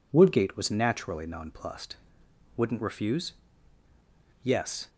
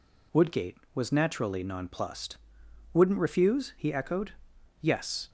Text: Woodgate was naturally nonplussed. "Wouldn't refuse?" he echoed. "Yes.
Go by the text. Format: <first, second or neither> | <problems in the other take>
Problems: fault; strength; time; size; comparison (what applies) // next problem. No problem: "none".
second | skips "he echoed"; at 3.8 s